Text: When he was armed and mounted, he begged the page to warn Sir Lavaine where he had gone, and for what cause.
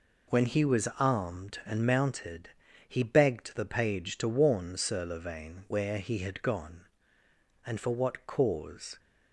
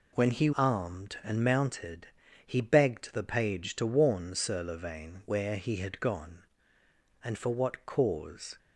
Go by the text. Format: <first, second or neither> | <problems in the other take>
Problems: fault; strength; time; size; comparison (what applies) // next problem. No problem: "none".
first | skips "was"; at 0.5 s